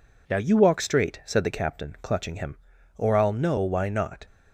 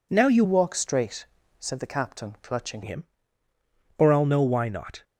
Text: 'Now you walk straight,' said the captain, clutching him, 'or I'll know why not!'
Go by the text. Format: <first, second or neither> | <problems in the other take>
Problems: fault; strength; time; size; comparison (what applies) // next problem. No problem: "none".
first | changes voice from "walk" to "clutching"; from 0.4 to 2.8 s; 2.4 s long